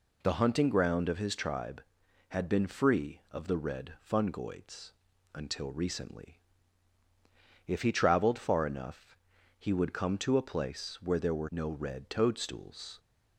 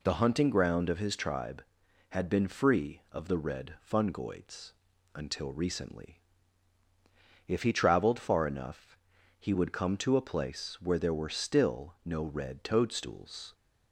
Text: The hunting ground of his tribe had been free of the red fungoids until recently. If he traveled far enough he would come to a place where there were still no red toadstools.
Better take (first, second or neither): second